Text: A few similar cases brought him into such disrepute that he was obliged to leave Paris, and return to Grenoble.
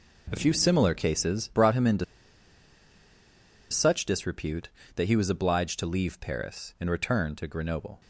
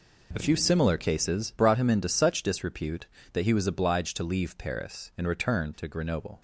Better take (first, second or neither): second